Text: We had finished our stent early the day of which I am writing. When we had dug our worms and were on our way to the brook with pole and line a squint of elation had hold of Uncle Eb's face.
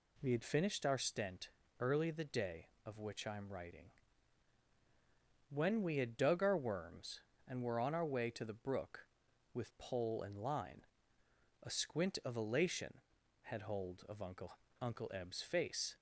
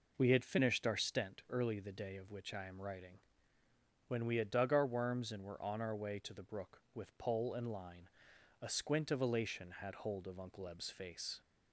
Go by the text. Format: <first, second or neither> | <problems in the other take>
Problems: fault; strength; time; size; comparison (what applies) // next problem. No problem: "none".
second | pauses between "stent" and "early"; slight; at 1.4 s; 0.30 s long // pauses between "line" and "a"; noticeable; at 10.8 s; 0.82 s long; noticeable in the second // says "Uncle" twice; at 14.8 s